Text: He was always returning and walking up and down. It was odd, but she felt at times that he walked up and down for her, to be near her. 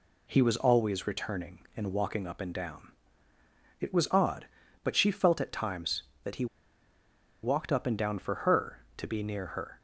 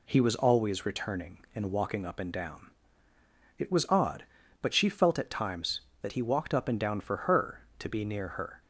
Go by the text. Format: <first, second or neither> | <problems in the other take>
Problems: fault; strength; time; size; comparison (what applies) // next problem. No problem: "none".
second | pauses between "he" and "walked"; at 6.4 s; 0.98 s long